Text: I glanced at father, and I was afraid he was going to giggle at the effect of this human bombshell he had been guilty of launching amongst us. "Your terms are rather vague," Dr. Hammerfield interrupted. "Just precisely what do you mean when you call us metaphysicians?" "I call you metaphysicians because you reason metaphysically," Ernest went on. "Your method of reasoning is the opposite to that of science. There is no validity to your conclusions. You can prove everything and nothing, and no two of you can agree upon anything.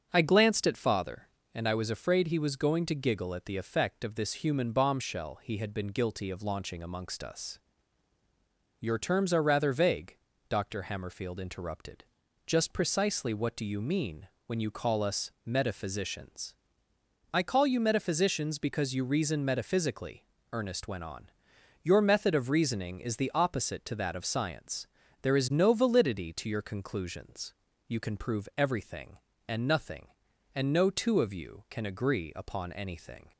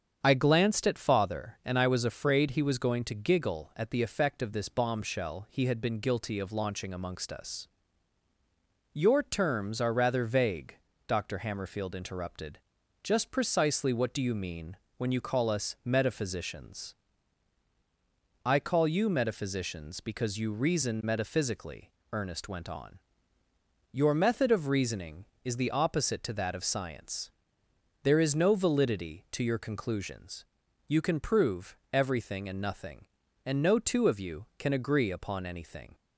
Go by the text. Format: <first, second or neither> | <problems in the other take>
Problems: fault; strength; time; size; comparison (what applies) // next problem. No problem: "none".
first | starts louder than the rest; strong; until 1.2 s; 7.5 dB; also in the first // skips "human"; at 4.6 s // pauses between "mean" and "when"; slight; at 14.7 s; 0.22 s long; slight in the first // pauses between "prove" and "everything"; slight; at 31.7 s; 0.16 s long